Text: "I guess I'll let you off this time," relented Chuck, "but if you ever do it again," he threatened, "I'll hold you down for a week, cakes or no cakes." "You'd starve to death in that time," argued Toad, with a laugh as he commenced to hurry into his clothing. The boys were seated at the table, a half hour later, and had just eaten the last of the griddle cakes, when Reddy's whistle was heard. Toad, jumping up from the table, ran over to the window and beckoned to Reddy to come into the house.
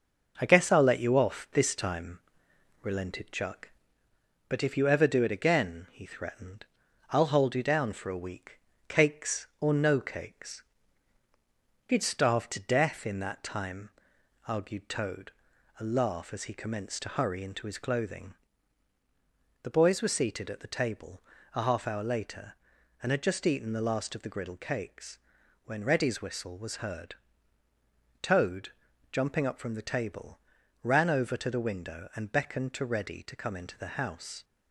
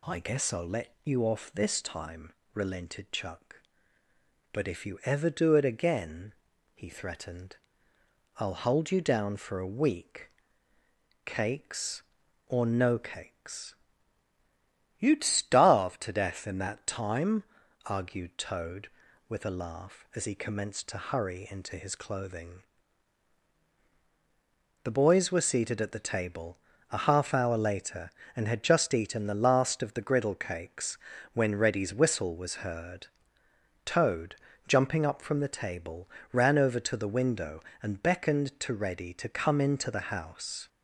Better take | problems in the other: second | skips "with"; at 15.5 s

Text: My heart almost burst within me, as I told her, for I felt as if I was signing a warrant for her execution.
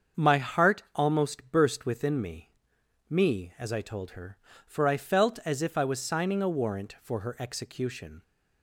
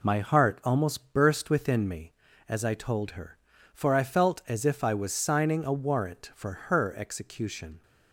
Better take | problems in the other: second | starts louder than the rest; until 1.2 s; 7 dB // says "me" twice; at 3.0 s

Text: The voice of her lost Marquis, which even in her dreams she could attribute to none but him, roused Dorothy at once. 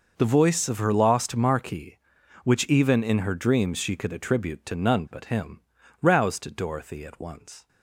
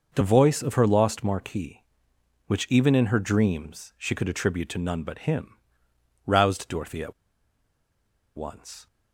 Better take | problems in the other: first | starts louder than the rest; noticeable; until 1.1 s; 6 dB // pauses between "at" and "once"; at 7.1 s; 1.2 s long

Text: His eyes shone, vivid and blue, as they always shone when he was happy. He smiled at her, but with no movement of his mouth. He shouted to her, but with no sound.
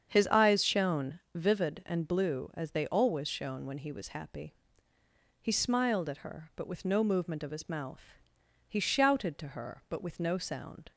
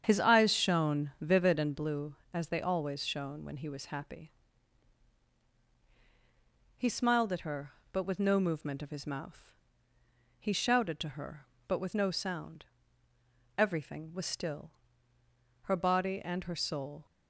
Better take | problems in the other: first | starts louder than the rest; strong; until 1.0 s; 8 dB; strong in the first // goes on to say "Everything was still her body and her soul"; strong; from 13.5 s on; 3.4 s long

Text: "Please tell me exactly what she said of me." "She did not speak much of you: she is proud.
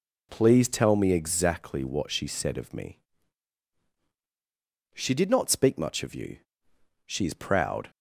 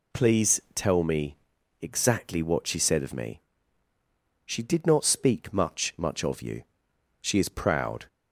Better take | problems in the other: first | pauses between "Please" and "tell"; slight; at 0.5 s; 0.16 s long // pauses between "me" and "exactly"; at 1.3 s; 0.44 s long // says "much" twice; at 5.9 s

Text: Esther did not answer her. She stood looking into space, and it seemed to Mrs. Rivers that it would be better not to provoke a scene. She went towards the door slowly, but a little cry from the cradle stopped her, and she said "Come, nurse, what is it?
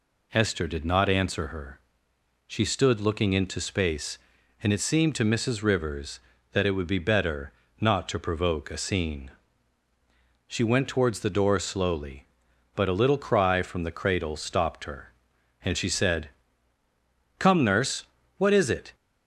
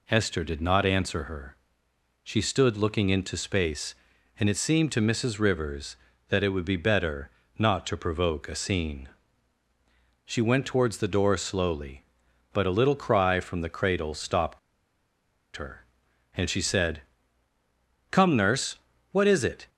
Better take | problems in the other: first | pauses between "better" and "not"; slight; at 7.3 s; 0.28 s long; slight in the first // pauses between "stopped" and "her"; noticeable; at 14.5 s; 0.97 s long // pauses between "said" and "Come"; at 17.0 s; 1.1 s long; also in the first

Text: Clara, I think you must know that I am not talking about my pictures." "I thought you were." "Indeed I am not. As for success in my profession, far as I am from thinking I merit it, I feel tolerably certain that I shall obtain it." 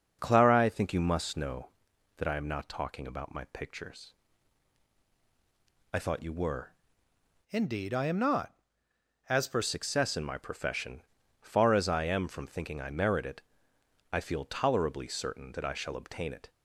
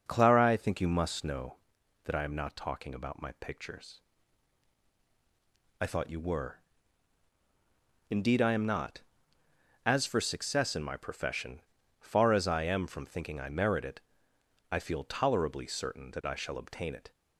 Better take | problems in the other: second | starts louder than the rest; until 1.2 s; 6.5 dB; noticeable in the second // changes voice from "Indeed" to "for"; from 7.4 to 9.6 s; 2.2 s long

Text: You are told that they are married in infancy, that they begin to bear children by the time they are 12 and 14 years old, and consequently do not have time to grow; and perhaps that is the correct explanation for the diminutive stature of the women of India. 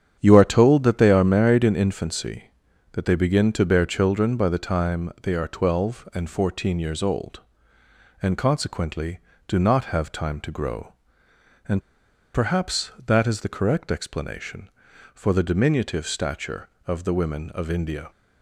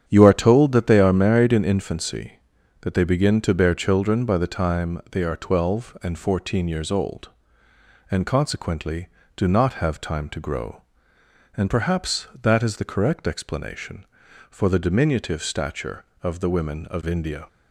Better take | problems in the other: second | starts louder than the rest; strong; until 1.2 s; 8.5 dB; strong in the second // pauses between "and" and "perhaps"; noticeable; at 11.7 s; 0.54 s long

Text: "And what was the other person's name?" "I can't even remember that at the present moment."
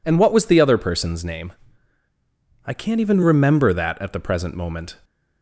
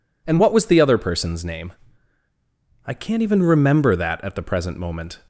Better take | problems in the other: neither | none

